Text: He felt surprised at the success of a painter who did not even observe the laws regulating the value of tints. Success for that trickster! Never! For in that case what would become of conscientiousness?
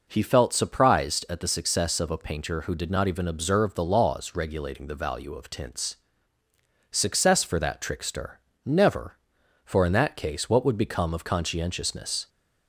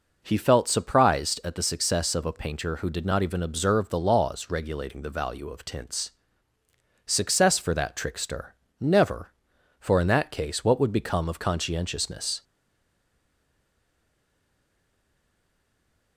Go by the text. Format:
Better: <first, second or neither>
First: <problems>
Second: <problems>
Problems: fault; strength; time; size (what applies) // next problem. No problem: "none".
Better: first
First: none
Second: stays silent after the last word; strong; from 12.4 s on; 3.7 s long